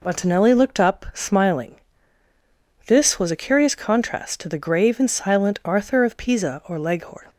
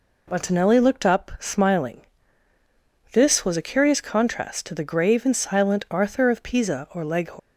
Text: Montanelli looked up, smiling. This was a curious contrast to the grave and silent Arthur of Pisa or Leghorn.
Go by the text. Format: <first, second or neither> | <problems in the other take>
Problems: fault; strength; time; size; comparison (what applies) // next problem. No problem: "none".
first | leaves "Leghorn" unfinished; at 7.3 s; 160 ms